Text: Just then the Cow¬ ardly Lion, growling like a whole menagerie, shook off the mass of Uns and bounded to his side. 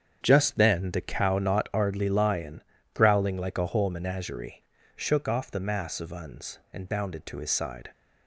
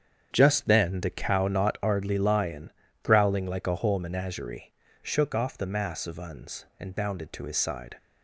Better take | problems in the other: neither | starts louder than the rest; strong; the same in both

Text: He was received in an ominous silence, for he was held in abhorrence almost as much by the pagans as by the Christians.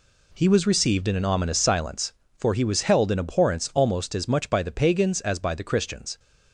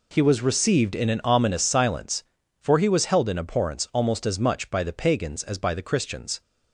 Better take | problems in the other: neither | none

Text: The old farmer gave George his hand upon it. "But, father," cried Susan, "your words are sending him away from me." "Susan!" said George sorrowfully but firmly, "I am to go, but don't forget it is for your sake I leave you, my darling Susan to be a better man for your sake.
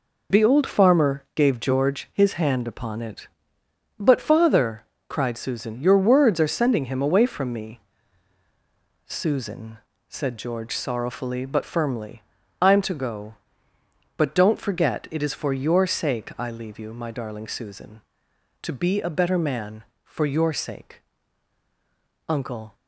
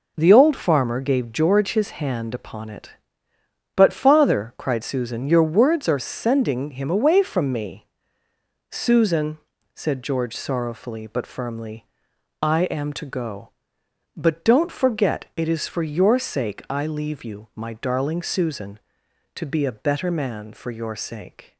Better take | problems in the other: second | goes on to say "Uncle"; slight; from 22.2 s on; 0.48 s long

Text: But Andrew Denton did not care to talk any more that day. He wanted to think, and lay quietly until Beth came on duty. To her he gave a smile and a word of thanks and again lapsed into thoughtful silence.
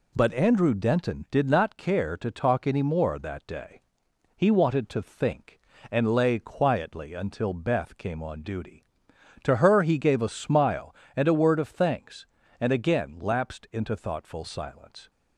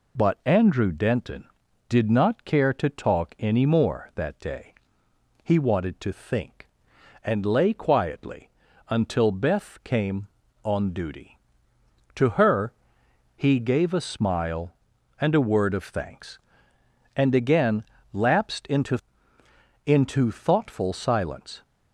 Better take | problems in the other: first | pauses between "quietly" and "until"; at 8.4 s; 0.40 s long // pauses between "her" and "he"; noticeable; at 12.7 s; 0.64 s long // pauses between "again" and "lapsed"; slight; at 17.8 s; 0.28 s long // says "into" twice; at 19.8 s

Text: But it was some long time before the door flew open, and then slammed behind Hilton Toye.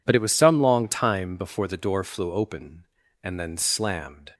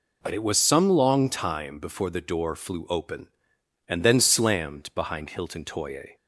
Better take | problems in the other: second | stops before "behind Hilton Toye"; at 4.3 s

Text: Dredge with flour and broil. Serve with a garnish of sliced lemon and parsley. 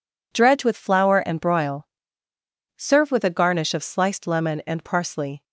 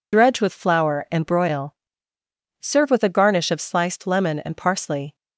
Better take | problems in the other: first | loses the start of "Dredge"; at 0.1 s; 35 ms

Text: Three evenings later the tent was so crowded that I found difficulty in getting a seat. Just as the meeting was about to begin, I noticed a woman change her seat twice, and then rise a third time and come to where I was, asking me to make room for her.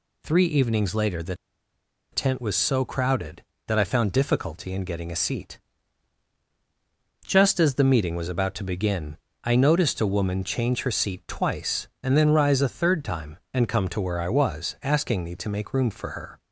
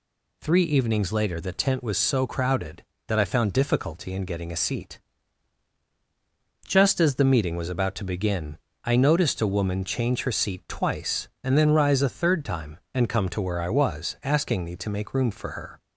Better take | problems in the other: second | pauses between "the" and "tent"; noticeable; at 1.3 s; 0.77 s long

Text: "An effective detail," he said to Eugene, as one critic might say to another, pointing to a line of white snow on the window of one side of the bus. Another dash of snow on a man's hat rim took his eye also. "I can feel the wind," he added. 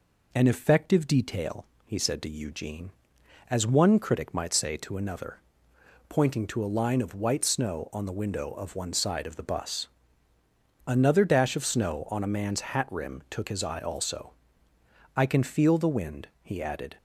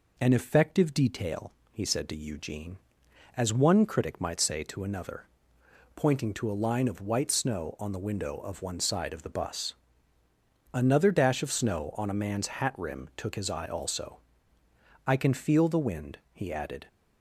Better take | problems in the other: neither | none

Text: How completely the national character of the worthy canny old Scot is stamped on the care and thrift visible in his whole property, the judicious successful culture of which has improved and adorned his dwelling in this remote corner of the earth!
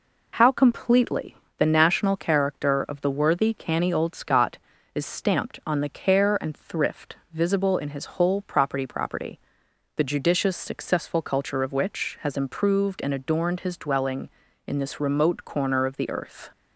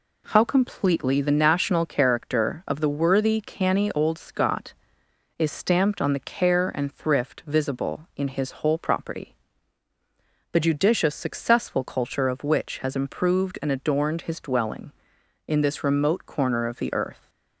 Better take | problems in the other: second | pauses between "completely" and "the"; slight; at 1.3 s; 0.22 s long // pauses between "thrift" and "visible"; slight; at 7.1 s; 0.18 s long // says "property" twice; at 8.8 s

